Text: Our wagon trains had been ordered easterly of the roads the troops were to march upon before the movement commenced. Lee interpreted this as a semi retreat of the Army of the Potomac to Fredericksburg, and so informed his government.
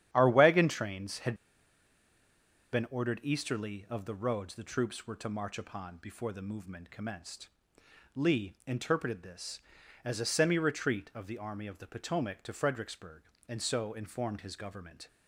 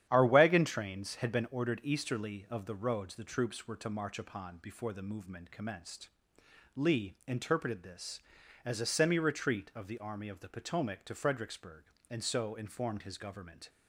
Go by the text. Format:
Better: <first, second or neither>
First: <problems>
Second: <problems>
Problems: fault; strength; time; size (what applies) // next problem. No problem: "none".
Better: second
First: starts louder than the rest; strong; until 1.1 s; 10.5 dB // pauses between "had" and "been"; strong; at 1.3 s; 1.3 s long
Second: starts louder than the rest; strong; until 1.1 s; 10.5 dB